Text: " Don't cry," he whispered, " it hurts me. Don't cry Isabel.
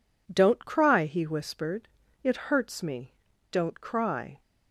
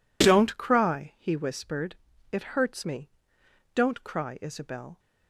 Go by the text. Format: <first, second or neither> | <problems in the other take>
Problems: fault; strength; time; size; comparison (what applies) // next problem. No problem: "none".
second | stops before "Isabel"; at 4.4 s